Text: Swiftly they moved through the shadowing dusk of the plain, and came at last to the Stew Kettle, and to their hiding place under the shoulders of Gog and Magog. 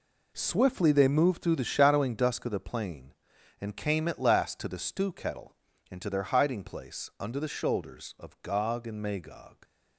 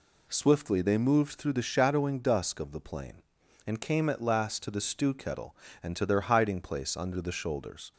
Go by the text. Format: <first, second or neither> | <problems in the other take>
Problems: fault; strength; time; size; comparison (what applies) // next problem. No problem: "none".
first | stops before "of Gog and Magog"; at 7.9 s